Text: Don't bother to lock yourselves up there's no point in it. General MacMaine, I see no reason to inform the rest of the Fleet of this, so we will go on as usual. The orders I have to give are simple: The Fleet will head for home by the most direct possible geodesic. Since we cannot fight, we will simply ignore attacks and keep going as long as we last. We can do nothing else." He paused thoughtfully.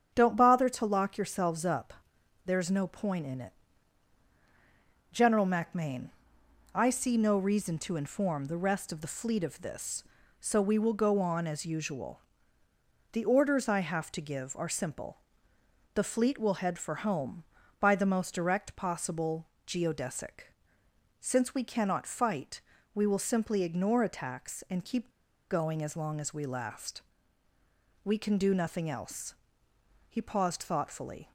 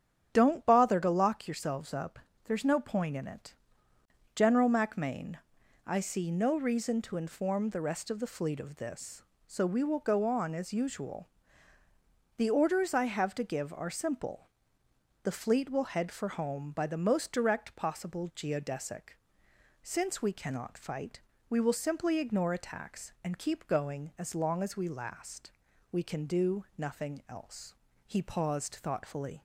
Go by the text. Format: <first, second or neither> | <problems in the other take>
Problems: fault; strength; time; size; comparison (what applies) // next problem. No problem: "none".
second | starts louder than the rest; strong; until 1.1 s; 8.5 dB; strong in the second // pauses between "up" and "there's"; noticeable; at 1.9 s; 0.52 s long; slight in the second // pauses between "possible" and "geodesic"; slight; at 19.4 s; 0.20 s long // pauses between "keep" and "going"; at 25.0 s; 0.42 s long